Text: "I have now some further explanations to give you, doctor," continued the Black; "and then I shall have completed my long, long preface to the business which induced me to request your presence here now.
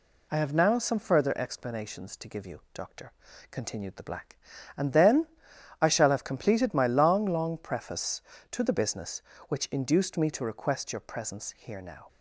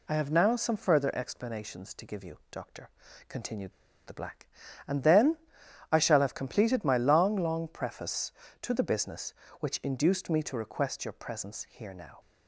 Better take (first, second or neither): first